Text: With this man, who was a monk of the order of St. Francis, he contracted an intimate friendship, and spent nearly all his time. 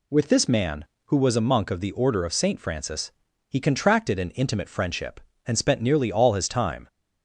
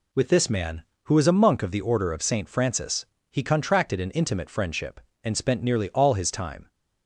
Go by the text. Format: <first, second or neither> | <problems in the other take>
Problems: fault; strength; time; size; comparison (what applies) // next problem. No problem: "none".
neither | none